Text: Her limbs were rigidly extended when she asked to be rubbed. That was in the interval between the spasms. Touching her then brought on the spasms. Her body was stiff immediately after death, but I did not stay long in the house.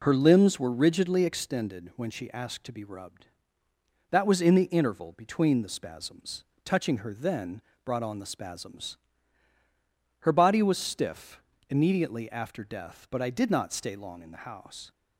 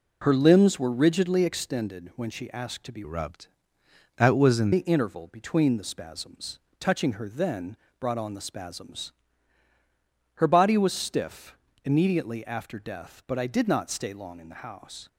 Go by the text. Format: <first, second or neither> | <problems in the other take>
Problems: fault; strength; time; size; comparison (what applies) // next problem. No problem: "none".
first | changes voice from "rubbed" to "in"; from 3.0 to 4.7 s; 1.7 s long // pauses between "then" and "brought"; slight; at 7.7 s; 0.24 s long; slight in the first // pauses between "stiff" and "immediately"; slight; at 11.5 s; 0.30 s long; slight in the first